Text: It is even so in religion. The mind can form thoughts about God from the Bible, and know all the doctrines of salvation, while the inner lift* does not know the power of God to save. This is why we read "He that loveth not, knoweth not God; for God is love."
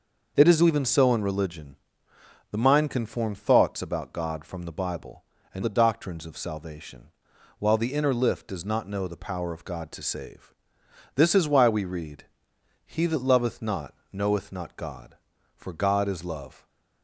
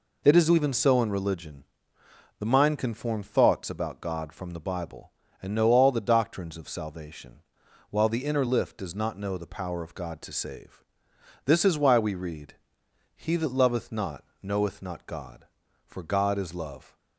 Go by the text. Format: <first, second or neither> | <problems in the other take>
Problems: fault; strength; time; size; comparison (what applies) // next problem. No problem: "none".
second | skips "know all"; at 5.6 s // pauses between "read" and "He"; noticeable; at 12.2 s; 0.60 s long; noticeable in the second // stays silent after the last word; slight; from 16.5 s on; 0.5 s long